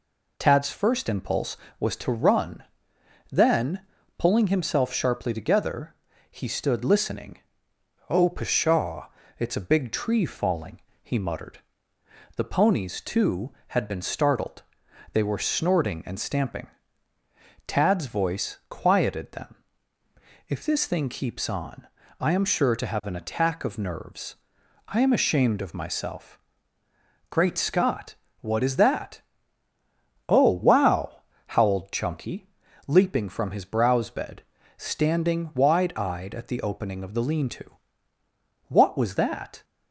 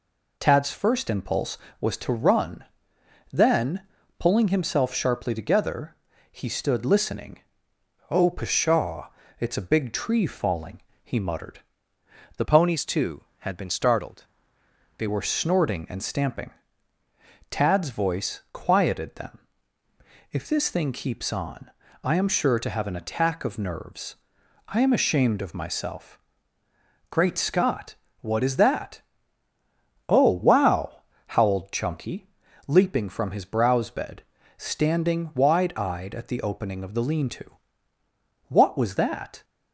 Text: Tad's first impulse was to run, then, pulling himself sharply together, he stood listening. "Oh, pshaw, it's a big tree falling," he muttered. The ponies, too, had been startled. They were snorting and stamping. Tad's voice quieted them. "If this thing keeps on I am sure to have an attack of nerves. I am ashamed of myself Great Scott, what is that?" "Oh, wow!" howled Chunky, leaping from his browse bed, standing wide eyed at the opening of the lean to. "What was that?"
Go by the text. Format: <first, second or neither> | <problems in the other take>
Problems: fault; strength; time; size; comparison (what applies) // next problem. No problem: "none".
first | changes voice from "ponies" to "They"; from 12.4 to 15.0 s; 2.6 s long // pauses between "on" and "I"; slight; at 21.6 s; 0.34 s long; slight in the first // pauses between "myself" and "Great"; noticeable; at 26.1 s; 0.90 s long; noticeable in the first